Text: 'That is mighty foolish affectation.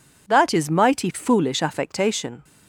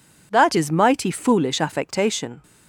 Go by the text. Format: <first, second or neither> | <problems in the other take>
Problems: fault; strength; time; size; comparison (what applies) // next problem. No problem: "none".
neither | none